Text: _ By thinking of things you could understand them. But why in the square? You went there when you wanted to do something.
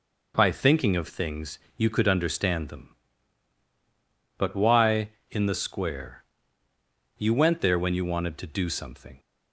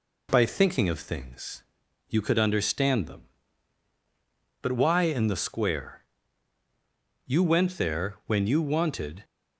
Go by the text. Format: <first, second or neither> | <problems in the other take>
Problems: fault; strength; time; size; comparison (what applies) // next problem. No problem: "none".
first | pauses between "things" and "you"; at 1.6 s; 0.44 s long; slight in the first // stops before "to do something"; at 9.2 s